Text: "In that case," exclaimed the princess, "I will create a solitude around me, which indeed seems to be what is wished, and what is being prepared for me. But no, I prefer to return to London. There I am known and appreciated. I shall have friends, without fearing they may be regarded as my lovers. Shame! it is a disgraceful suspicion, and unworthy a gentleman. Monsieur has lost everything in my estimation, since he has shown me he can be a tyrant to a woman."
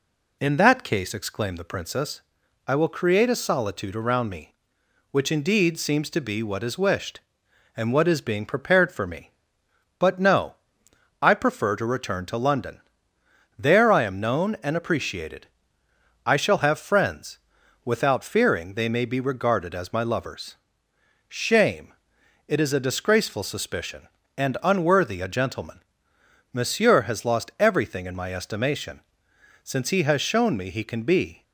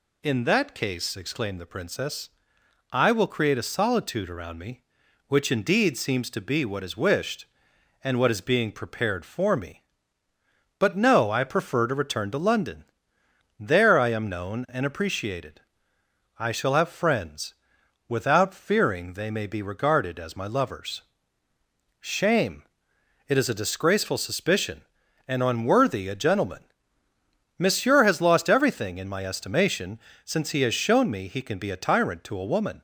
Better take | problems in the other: second | stops before "a tyrant to a woman"; at 31.4 s

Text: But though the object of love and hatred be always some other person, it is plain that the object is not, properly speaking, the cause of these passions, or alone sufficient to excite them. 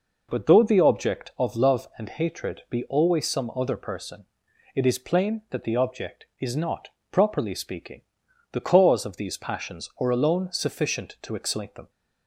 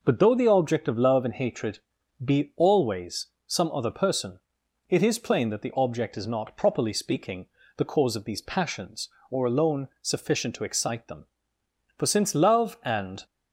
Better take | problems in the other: first | pauses between "hatred" and "be"; at 1.7 s; 0.44 s long // pauses between "always" and "some"; slight; at 3.2 s; 0.18 s long // goes on to say "For since love and"; noticeable; from 11.9 s on; 1.2 s long

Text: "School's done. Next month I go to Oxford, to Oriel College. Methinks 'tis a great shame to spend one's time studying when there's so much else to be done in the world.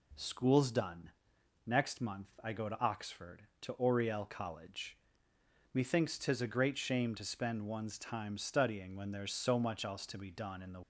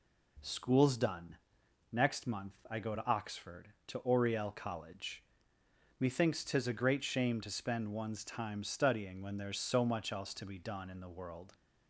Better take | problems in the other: second | pauses between "month" and "I"; slight; at 2.2 s; 0.15 s long; slight in the second // stops before "world"; at 10.8 s

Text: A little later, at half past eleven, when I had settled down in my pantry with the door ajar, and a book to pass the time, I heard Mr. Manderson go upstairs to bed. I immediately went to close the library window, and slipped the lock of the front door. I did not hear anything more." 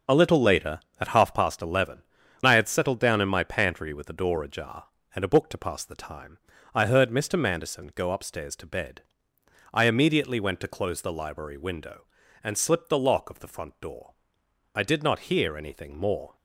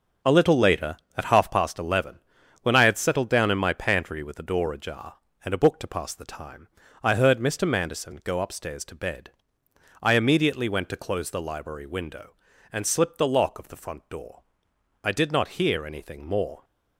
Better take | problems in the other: second | starts louder than the rest; until 1.2 s; 6 dB // skips "when"; at 2.2 s

